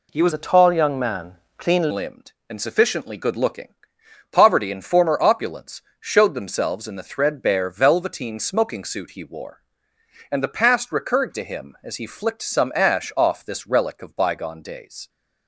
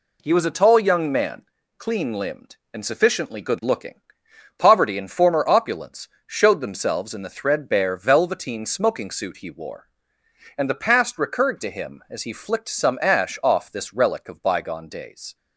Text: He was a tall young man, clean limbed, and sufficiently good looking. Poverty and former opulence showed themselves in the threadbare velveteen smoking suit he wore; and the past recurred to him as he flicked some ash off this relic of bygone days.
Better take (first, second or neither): second